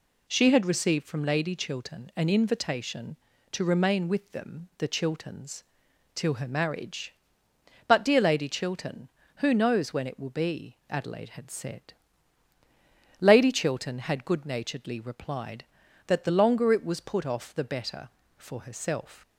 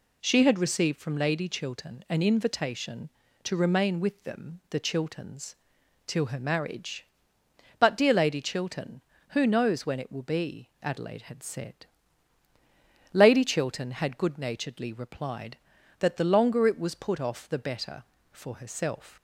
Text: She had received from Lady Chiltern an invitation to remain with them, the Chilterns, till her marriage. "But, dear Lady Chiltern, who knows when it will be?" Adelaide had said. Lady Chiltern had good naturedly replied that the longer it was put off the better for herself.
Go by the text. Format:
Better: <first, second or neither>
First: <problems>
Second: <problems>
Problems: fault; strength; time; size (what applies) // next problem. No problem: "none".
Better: neither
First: none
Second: none